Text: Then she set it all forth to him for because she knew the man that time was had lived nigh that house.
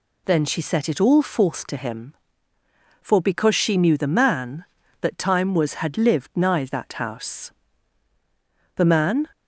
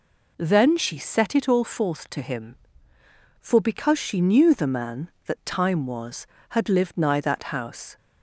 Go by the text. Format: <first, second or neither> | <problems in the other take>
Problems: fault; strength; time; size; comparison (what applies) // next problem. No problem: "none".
second | goes on to say "The man"; from 8.7 s on; 0.52 s long